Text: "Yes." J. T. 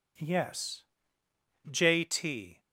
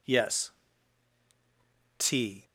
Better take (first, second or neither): first